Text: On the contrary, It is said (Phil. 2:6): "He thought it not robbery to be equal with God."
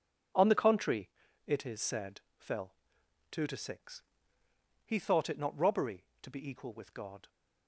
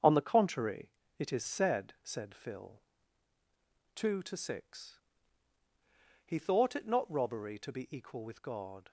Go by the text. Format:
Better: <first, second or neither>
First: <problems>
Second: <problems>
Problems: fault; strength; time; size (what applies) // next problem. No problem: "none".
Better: first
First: none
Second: starts louder than the rest; strong; until 1.2 s; 7.5 dB // says "said" twice; at 2.0 s